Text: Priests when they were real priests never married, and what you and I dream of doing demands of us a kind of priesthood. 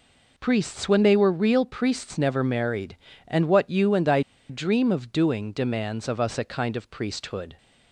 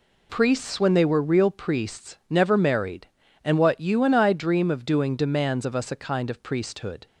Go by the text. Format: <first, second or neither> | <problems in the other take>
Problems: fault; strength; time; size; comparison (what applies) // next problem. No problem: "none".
second | pauses between "I" and "dream"; slight; at 4.2 s; 0.29 s long